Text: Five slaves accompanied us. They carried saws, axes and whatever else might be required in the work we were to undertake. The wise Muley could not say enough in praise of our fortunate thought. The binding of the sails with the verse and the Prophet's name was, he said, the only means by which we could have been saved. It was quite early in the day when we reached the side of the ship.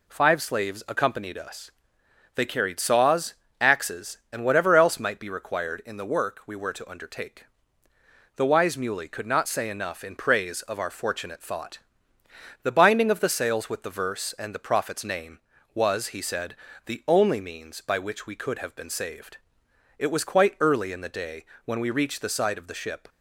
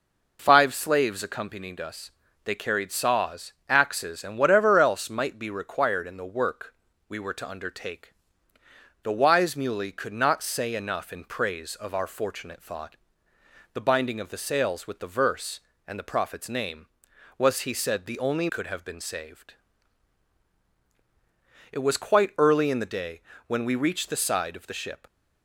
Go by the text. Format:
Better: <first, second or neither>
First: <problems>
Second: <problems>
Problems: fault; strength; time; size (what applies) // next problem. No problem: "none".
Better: first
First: pauses between "day" and "when"; slight; at 21.4 s; 0.18 s long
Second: pauses between "work" and "we"; slight; at 6.7 s; 0.36 s long // skips "means by which we"; at 18.4 s // pauses between "day" and "when"; slight; at 23.1 s; 0.26 s long